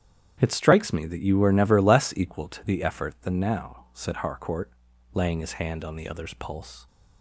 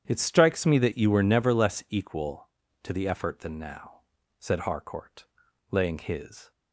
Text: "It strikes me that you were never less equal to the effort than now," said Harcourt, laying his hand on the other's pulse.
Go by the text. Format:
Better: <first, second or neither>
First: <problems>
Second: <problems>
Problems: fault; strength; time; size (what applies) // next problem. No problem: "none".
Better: first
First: starts louder than the rest; strong; until 1.4 s; 9.5 dB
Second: starts louder than the rest; strong; until 1.0 s; 9 dB // stops before "hand on the other's pulse"; at 6.5 s